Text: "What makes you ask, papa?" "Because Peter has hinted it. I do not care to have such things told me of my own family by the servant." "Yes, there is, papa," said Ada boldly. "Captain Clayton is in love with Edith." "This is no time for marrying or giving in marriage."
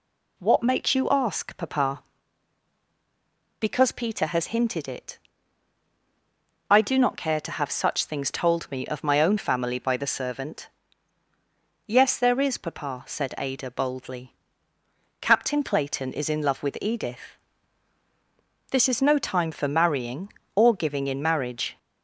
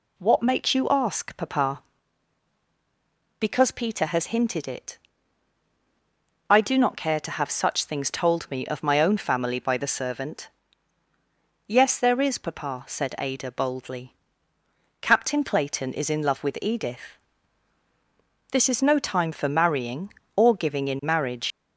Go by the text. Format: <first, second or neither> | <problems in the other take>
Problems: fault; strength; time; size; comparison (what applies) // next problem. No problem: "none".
first | leaves "marriage" unfinished; at 21.5 s; 110 ms